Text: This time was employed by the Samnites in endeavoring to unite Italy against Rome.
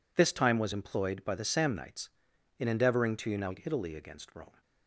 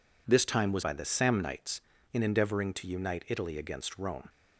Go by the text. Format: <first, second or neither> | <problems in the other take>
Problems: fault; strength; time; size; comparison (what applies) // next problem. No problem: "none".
first | skips "employed"; at 0.8 s